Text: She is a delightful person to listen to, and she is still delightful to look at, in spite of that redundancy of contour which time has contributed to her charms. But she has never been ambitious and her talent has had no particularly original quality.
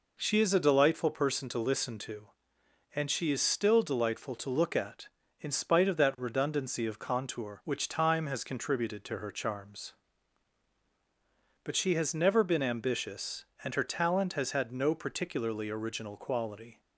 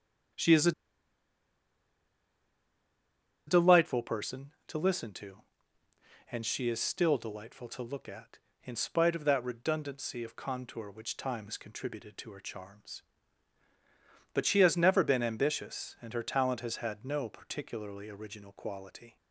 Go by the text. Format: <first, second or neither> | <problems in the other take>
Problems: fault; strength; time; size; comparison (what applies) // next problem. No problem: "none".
first | starts louder than the rest; strong; until 4.1 s; 9.5 dB // pauses between "a" and "delightful"; strong; at 0.7 s; 2.7 s long